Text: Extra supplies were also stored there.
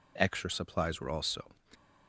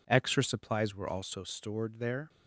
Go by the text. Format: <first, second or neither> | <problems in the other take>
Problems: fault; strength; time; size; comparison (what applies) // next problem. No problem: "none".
second | stops before "stored there"; at 1.7 s